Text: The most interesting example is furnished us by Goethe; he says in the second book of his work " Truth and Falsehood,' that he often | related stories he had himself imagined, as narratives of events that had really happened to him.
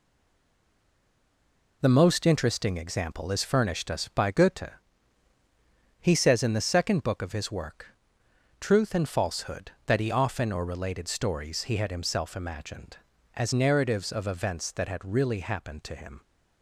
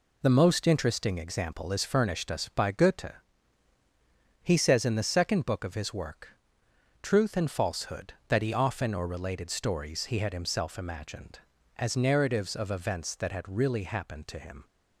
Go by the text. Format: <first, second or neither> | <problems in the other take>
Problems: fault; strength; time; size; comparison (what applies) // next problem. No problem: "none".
second | stays silent before the first word; noticeable; until 1.8 s; 1.8 s long